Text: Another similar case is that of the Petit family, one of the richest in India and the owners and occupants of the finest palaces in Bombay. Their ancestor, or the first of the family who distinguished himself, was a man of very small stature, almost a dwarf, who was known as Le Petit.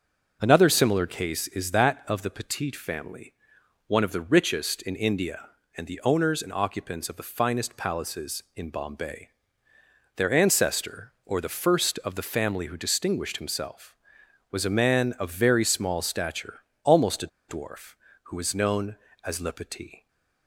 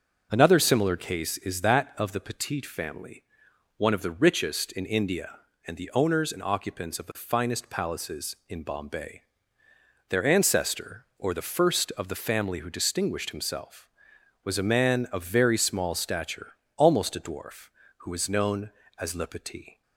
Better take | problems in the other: second | starts louder than the rest; until 1.4 s; 6.5 dB; also in the second // pauses between "a" and "dwarf"; slight; at 17.2 s; 0.21 s long // stays silent after the last word; slight; from 19.9 s on; 0.5 s long

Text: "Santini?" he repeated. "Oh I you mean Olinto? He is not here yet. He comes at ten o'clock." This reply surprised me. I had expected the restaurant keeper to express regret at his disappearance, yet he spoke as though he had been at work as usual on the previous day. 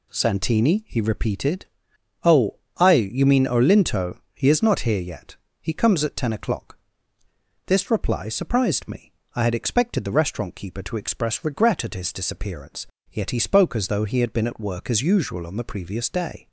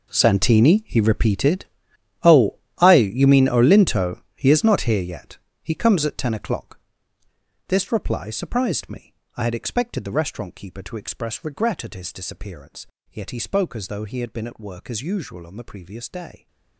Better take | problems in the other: first | gets quieter; strong; throughout; 16.5 dB // pauses between "Oh" and "I"; slight; at 2.5 s; 0.24 s long; slight in the first

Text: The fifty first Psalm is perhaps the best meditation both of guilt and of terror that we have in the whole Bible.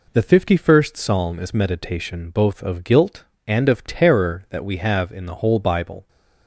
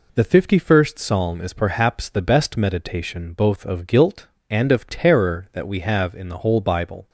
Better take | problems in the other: second | skips "perhaps the best"; at 1.5 s

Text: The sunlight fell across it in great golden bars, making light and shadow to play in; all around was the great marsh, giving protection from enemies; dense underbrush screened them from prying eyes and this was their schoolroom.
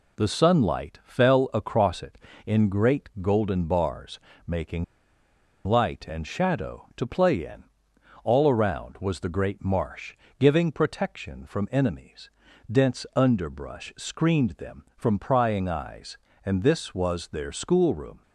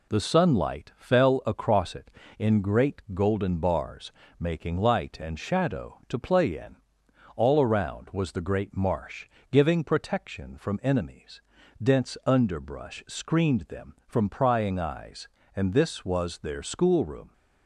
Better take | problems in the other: second | pauses between "making" and "light"; noticeable; at 4.8 s; 0.81 s long

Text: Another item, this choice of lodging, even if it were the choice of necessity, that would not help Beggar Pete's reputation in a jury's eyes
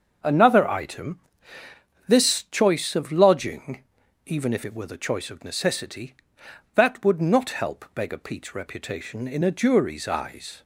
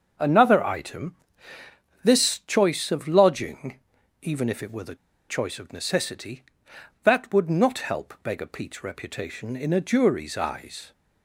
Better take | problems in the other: first | starts louder than the rest; until 2.0 s; 6.5 dB; also in the first // pauses between "the" and "choice"; slight; at 4.9 s; 0.33 s long

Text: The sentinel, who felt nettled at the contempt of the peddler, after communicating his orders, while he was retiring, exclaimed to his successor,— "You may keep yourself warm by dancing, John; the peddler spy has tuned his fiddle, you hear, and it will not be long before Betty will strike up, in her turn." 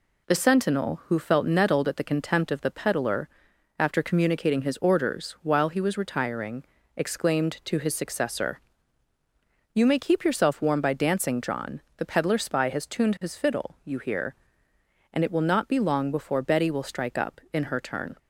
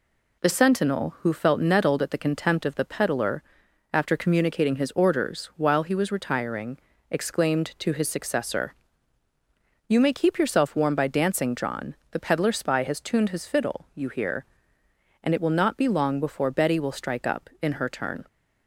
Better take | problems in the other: neither | none

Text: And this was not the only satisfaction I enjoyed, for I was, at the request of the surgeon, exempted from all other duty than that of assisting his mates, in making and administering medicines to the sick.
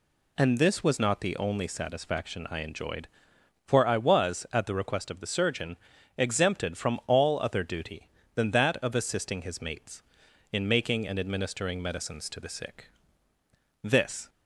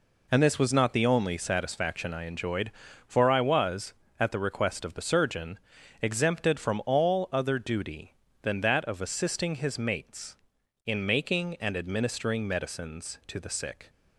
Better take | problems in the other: second | goes on to say "This"; slight; from 13.8 s on; 0.46 s long

